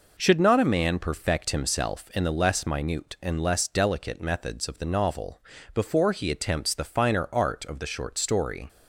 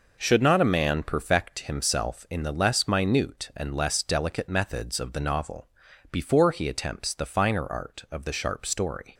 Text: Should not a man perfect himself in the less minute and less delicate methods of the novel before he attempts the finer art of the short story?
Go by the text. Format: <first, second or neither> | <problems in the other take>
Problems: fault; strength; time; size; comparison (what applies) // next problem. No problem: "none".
first | pauses between "novel" and "before"; at 5.6 s; 0.42 s long; slight in the first // says "sharp" for "short"; at 8.3 s